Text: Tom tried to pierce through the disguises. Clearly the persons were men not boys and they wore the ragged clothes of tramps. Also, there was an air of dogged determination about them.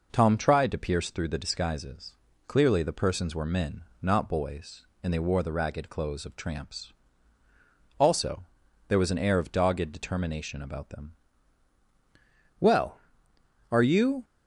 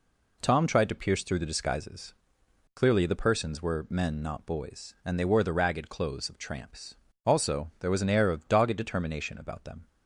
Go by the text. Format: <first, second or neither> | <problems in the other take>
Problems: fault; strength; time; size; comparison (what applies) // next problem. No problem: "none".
second | pauses between "men" and "not"; slight; at 3.8 s; 0.20 s long // goes on to say "Well are you"; from 12.5 s on; 1.6 s long